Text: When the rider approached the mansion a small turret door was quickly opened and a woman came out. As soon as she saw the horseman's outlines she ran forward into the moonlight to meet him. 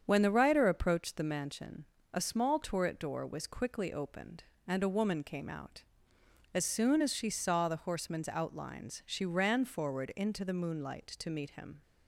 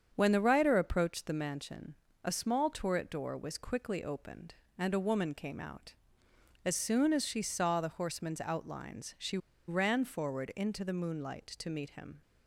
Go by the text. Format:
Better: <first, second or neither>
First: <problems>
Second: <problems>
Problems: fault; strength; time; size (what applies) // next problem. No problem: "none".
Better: first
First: starts louder than the rest; strong; until 1.0 s; 7.5 dB // pauses between "mansion" and "a"; slight; at 1.8 s; 0.28 s long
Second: starts louder than the rest; strong; until 1.1 s; 7.5 dB // pauses between "mansion" and "a"; slight; at 1.9 s; 0.30 s long // pauses between "she" and "ran"; slight; at 9.3 s; 0.30 s long